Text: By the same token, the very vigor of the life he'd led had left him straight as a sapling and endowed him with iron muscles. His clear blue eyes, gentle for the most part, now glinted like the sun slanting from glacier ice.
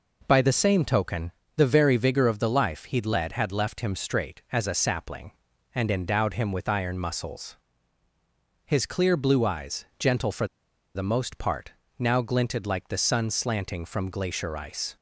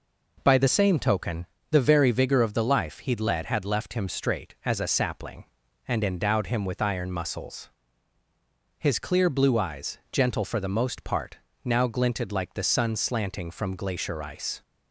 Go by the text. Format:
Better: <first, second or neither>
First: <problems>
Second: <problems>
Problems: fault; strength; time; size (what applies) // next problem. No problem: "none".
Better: second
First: pauses between "for" and "the"; noticeable; at 10.4 s; 0.48 s long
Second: none